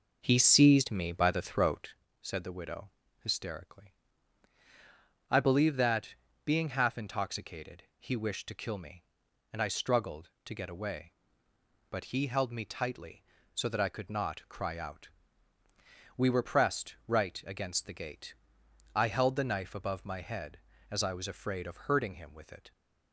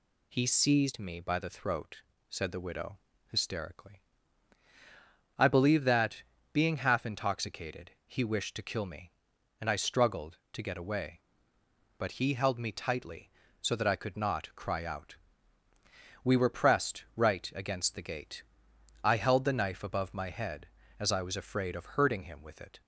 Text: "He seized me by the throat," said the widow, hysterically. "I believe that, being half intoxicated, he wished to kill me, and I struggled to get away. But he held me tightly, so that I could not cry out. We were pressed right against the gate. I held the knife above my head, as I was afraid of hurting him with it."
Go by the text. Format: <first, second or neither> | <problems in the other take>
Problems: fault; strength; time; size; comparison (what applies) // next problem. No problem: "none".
second | starts louder than the rest; noticeable; until 2.0 s; 5.5 dB